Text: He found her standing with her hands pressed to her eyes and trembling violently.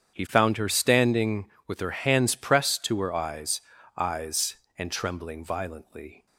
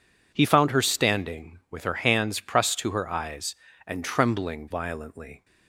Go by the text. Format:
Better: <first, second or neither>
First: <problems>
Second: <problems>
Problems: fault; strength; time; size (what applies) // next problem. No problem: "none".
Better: second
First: starts louder than the rest; strong; until 1.1 s; 8.5 dB // says "eyes" twice; at 3.9 s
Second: none